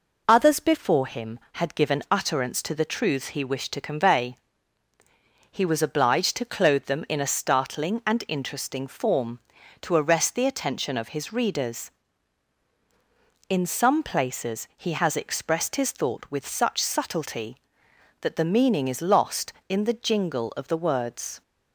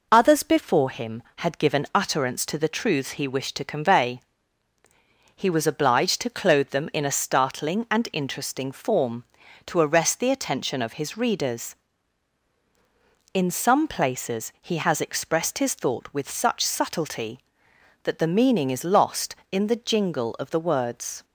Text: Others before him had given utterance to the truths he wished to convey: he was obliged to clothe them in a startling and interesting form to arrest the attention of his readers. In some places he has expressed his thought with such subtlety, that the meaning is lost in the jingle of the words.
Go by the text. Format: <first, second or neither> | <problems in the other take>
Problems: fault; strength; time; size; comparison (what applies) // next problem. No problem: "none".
neither | none